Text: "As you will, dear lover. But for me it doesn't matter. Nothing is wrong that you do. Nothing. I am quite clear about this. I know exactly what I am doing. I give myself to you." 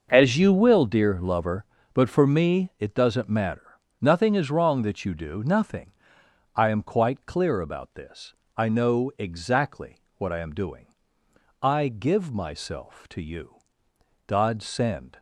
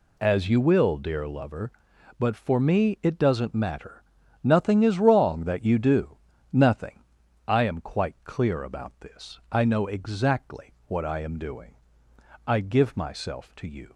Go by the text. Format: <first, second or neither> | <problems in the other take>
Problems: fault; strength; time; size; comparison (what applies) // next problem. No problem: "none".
second | starts louder than the rest; noticeable; until 1.1 s; 6 dB // pauses between "exactly" and "what"; slight; at 9.9 s; 0.18 s long // goes on to say "God send"; noticeable; from 14.2 s on; 0.94 s long